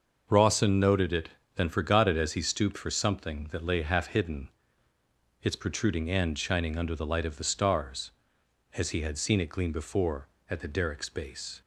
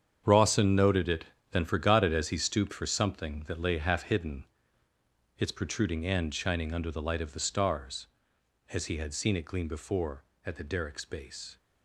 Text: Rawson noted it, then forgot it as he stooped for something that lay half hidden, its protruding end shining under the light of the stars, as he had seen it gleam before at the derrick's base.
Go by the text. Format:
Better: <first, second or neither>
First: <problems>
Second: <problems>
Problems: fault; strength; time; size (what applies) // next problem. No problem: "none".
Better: first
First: starts louder than the rest; noticeable; until 1.5 s; 6 dB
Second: gets quieter; strong; throughout; 11.5 dB // starts louder than the rest; strong; until 1.5 s; 8 dB